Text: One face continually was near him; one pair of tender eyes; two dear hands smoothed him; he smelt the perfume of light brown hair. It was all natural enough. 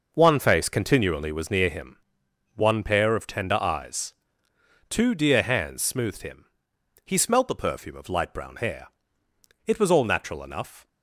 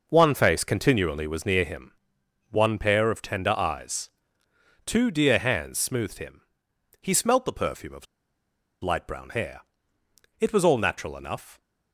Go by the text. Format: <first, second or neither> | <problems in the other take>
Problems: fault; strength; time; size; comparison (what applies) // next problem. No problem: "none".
first | pauses between "of" and "light"; noticeable; at 8.0 s; 0.77 s long